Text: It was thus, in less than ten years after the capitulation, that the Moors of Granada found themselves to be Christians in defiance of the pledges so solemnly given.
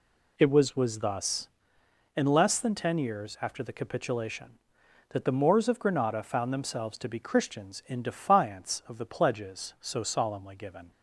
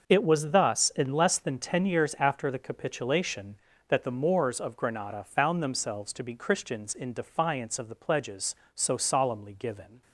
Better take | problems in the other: second | says "was" twice; at 0.7 s

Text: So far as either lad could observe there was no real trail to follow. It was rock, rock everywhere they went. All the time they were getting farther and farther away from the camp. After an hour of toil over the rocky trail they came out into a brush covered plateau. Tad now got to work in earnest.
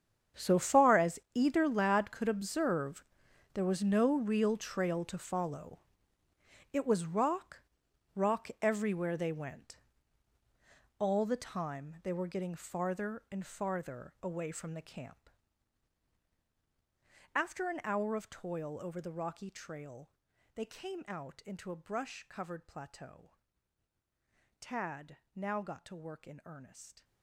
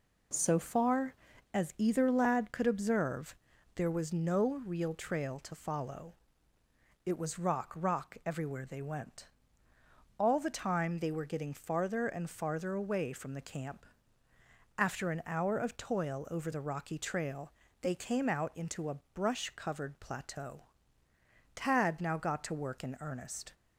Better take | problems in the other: second | gets quieter; strong; throughout; 16.5 dB // pauses between "as" and "either"; slight; at 1.1 s; 0.16 s long // pauses between "observe" and "there"; noticeable; at 3.0 s; 0.48 s long; also in the second // pauses between "trail" and "they"; noticeable; at 20.0 s; 0.46 s long; slight in the second // pauses between "Tad" and "now"; slight; at 25.1 s; 0.16 s long

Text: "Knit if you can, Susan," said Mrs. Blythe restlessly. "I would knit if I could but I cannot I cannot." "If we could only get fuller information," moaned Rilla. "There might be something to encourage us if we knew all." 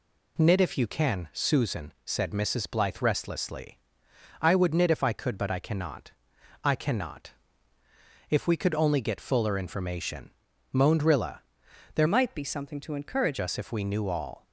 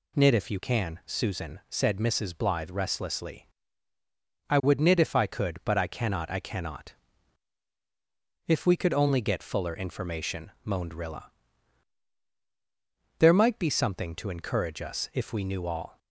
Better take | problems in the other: second | pauses between "cannot" and "I"; noticeable; at 6.1 s; 0.52 s long // changes voice from "might" to "encourage"; from 12.0 to 13.3 s; 1.3 s long

